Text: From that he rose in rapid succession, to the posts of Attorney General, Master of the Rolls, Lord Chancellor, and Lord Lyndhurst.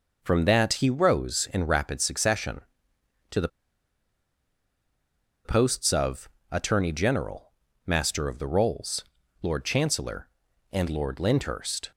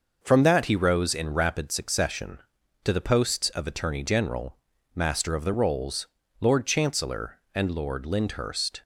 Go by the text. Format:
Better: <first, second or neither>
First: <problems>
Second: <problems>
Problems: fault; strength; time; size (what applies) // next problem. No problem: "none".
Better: second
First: pauses between "the" and "posts"; strong; at 3.4 s; 1.9 s long // pauses between "of" and "Attorney"; slight; at 6.2 s; 0.24 s long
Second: none